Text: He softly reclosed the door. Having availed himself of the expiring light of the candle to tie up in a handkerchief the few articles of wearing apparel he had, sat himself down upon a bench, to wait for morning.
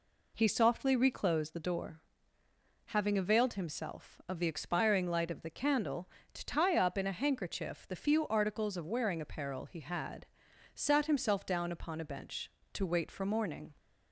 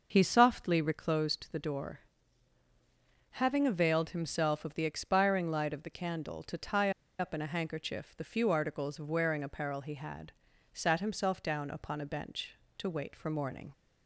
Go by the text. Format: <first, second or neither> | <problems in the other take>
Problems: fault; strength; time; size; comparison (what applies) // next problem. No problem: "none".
first | starts louder than the rest; noticeable; until 1.1 s; 6 dB // pauses between "tie" and "up"; slight; at 6.9 s; 0.28 s long